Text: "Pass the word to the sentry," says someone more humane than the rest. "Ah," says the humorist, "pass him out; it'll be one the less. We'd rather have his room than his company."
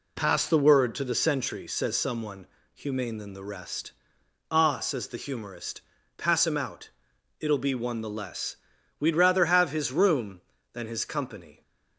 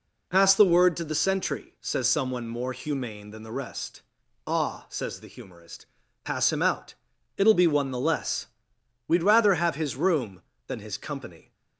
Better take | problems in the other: second | skips "more"; at 2.6 s

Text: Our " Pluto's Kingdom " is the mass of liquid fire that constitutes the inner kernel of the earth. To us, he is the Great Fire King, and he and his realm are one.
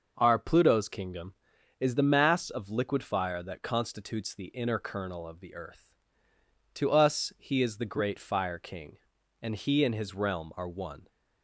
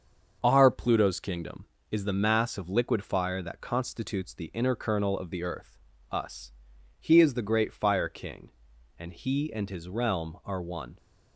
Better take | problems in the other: first | starts louder than the rest; until 1.4 s; 6.5 dB; also in the first // skips "To"; at 5.9 s

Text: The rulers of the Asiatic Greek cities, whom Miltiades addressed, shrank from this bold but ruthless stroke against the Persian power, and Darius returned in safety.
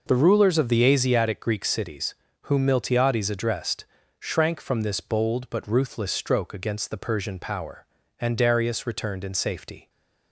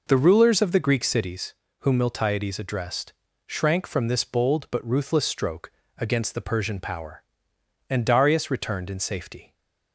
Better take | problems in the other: first | skips "Asiatic"; at 0.7 s // pauses between "stroke" and "against"; slight; at 5.6 s; 0.28 s long

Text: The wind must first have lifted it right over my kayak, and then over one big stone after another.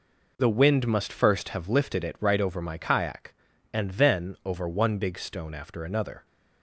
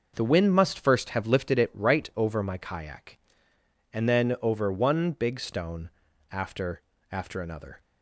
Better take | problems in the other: first | pauses between "stone" and "after"; at 5.9 s; 0.40 s long // says "after" twice; at 7.1 s

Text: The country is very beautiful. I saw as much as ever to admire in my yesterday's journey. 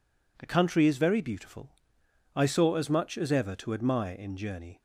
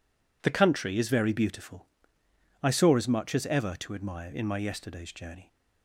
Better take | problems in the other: second | skips "my yesterday's"; at 4.3 s

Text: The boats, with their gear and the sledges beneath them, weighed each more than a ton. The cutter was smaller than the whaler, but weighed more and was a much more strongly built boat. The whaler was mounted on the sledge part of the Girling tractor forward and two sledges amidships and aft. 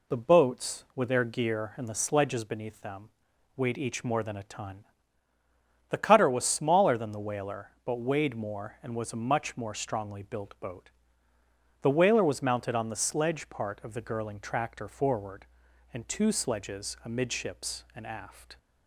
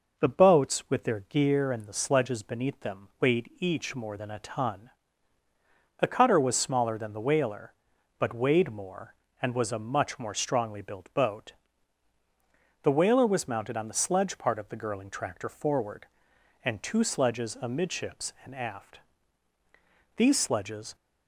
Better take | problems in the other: first | goes on to say "These sledges"; noticeable; from 20.1 s on; 0.78 s long

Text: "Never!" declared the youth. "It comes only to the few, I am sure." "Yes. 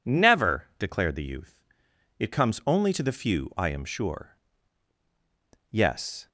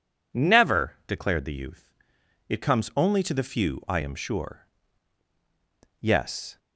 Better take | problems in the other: neither | none

